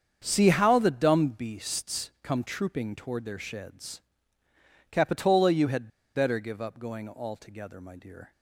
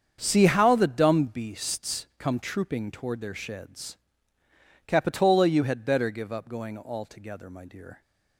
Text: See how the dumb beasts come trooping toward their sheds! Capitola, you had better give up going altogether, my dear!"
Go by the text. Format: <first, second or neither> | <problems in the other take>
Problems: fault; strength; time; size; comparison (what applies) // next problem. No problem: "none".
second | starts louder than the rest; strong; until 1.2 s; 7.5 dB; strong in the second // pauses between "had" and "better"; slight; at 5.8 s; 0.26 s long